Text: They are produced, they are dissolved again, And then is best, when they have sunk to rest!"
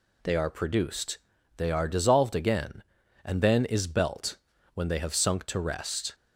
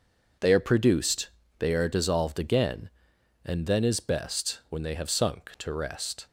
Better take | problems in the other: second | says "belt" for "best"; at 3.8 s

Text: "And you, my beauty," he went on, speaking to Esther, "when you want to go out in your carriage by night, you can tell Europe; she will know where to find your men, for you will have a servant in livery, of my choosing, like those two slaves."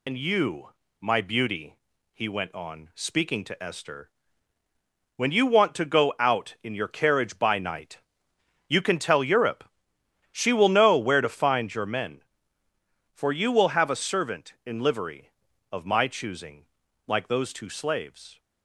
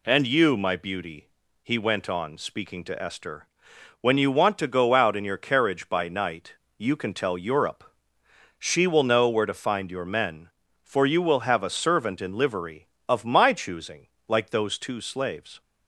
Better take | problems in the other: second | loses the start of "And"; at 0.0 s; 85 ms

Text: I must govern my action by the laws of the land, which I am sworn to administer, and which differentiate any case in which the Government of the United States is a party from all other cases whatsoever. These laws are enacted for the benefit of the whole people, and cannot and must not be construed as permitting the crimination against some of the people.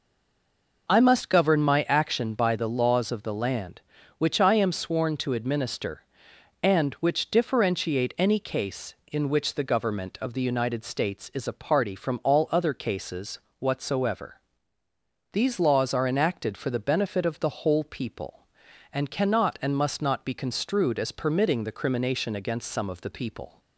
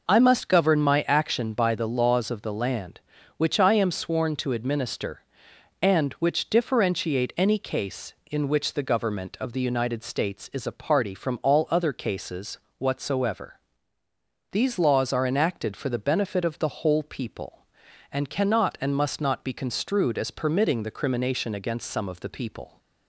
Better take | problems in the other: second | stays silent before the first word; slight; until 0.8 s; 0.8 s long // pauses between "cases" and "whatsoever"; slight; at 13.3 s; 0.22 s long; slight in the second

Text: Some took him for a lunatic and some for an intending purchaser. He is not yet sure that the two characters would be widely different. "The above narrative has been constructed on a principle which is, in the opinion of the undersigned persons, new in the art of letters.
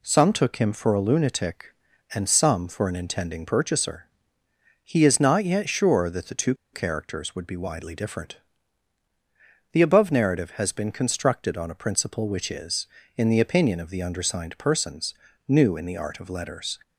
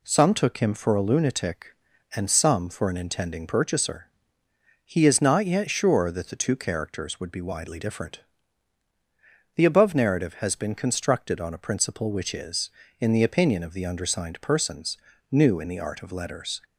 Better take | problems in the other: second | pauses between "two" and "characters"; slight; at 6.5 s; 0.19 s long

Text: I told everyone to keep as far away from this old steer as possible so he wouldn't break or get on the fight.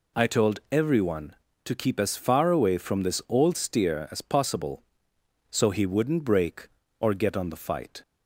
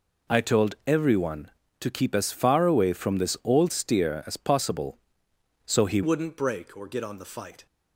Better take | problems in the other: first | changes voice at "wouldn't"; from 6.0 s on; 1.6 s long

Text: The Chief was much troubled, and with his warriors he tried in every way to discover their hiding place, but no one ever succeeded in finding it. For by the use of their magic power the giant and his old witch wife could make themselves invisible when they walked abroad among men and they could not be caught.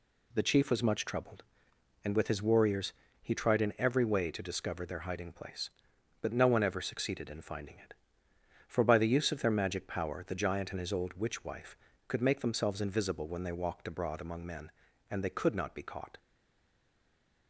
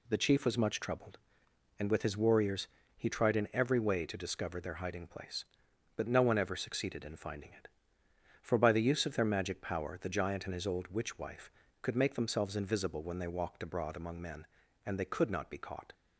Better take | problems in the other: second | pauses between "warriors" and "he"; slight; at 2.9 s; 0.28 s long; slight in the second // stays silent after the last word; noticeable; from 16.1 s on; 1.3 s long

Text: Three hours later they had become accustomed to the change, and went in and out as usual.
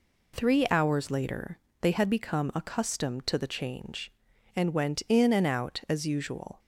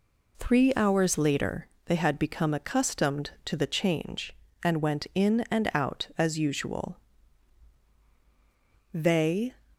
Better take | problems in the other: first | pauses between "later" and "they"; slight; at 1.6 s; 0.18 s long; slight in the first // goes on to say "They"; noticeable; from 8.9 s on; 0.62 s long

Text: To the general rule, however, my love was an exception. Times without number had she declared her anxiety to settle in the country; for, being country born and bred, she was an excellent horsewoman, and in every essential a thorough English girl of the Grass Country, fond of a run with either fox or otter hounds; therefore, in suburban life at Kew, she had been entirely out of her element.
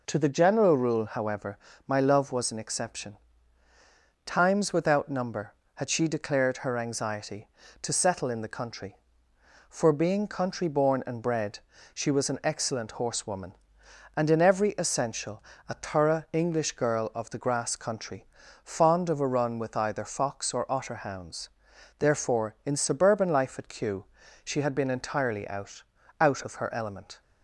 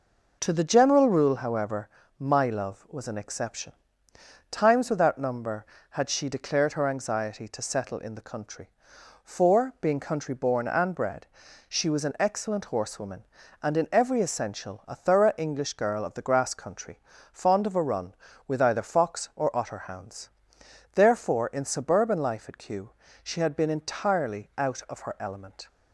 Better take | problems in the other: second | pauses between "essential" and "a"; slight; at 15.4 s; 0.24 s long // says "out" twice; at 26.2 s

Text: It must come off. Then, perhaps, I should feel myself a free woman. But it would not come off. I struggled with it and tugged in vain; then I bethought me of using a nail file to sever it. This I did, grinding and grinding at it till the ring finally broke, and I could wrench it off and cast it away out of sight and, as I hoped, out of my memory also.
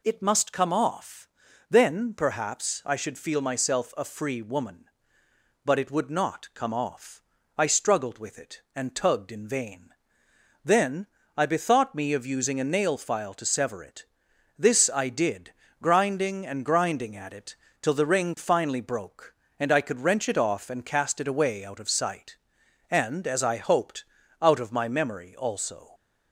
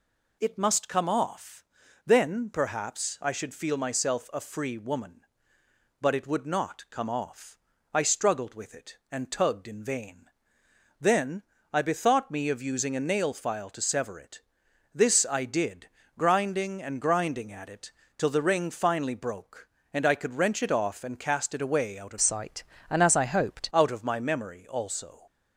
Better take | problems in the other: first | pauses between "then" and "I"; slight; at 11.4 s; 0.30 s long; slight in the first // pauses between "it" and "till"; slight; at 17.9 s; 0.28 s long; slight in the first // changes voice from "sight" to "hoped"; from 22.2 to 23.6 s; 1.4 s long

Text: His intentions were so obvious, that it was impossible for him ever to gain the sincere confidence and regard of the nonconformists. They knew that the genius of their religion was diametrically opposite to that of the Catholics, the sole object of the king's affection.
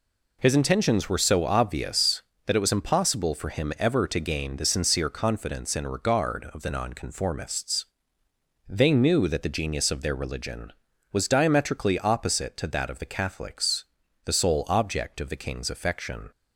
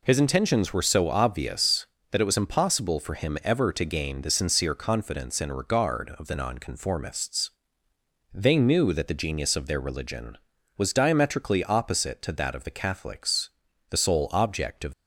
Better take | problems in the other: first | stops before "the king's affection"; at 14.9 s

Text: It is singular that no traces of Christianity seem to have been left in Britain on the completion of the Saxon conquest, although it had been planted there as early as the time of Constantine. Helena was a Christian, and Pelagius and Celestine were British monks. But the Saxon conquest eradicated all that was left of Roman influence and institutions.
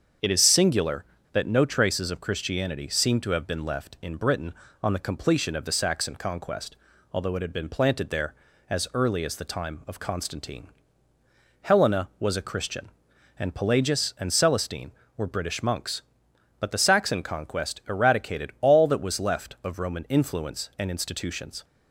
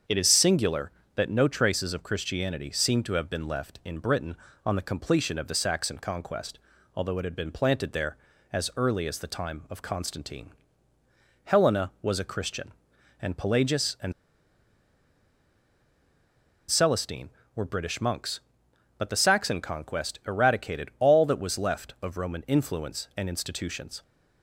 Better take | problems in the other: first | starts louder than the rest; until 1.3 s; 7 dB; also in the first // pauses between "and" and "Celestine"; strong; at 14.1 s; 2.5 s long

